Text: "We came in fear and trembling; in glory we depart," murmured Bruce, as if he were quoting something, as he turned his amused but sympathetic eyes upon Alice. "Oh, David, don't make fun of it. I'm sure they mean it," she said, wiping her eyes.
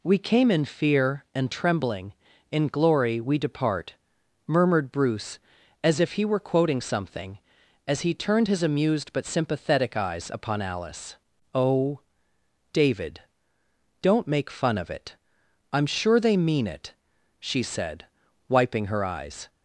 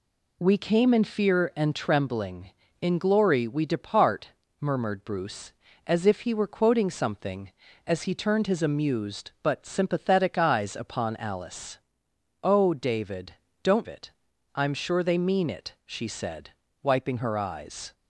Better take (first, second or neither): first